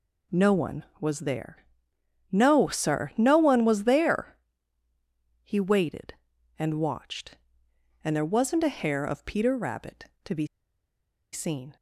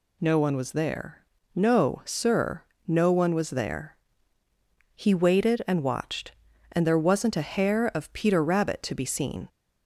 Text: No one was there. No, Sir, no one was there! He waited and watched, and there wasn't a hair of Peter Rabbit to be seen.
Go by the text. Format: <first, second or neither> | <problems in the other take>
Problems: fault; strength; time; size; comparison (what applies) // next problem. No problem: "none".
second | pauses between "be" and "seen"; noticeable; at 10.4 s; 0.88 s long